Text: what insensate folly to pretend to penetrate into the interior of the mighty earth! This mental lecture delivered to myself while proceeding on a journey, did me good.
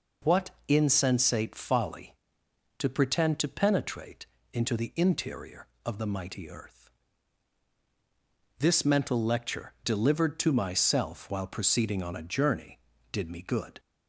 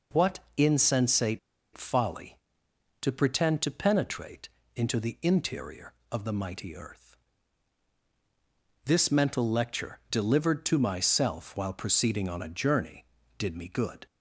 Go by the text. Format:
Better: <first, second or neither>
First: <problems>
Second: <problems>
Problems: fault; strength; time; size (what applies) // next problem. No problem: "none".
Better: first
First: pauses between "what" and "insensate"; slight; at 0.5 s; 0.18 s long // pauses between "penetrate" and "into"; slight; at 4.2 s; 0.28 s long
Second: pauses between "what" and "insensate"; slight; at 0.3 s; 0.18 s long // pauses between "insensate" and "folly"; at 1.3 s; 0.36 s long // pauses between "penetrate" and "into"; slight; at 4.4 s; 0.28 s long